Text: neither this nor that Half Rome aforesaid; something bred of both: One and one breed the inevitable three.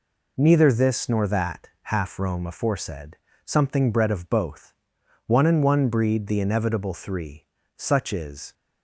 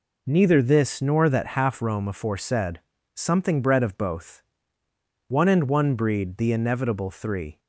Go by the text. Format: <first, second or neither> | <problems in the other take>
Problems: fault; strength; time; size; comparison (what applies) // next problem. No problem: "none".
second | goes on to say "Such is"; noticeable; from 7.7 s on; 0.76 s long